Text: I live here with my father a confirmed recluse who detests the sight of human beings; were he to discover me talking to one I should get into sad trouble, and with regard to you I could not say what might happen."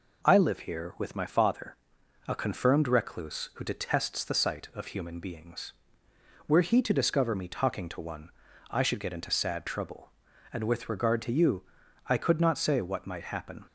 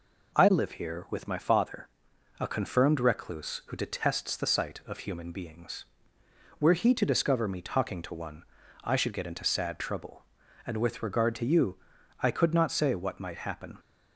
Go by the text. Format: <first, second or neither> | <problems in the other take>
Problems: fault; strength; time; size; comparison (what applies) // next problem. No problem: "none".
neither | pauses between "father" and "a"; noticeable; the same in both // pauses between "one" and "I"; the same in both // pauses between "you" and "I"; the same in both